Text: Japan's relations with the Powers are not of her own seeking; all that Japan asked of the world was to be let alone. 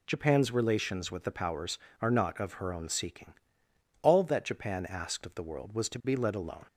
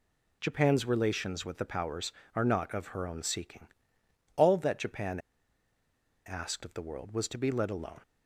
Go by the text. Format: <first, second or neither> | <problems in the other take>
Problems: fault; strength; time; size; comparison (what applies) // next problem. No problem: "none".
first | pauses between "Japan" and "asked"; at 5.1 s; 1.0 s long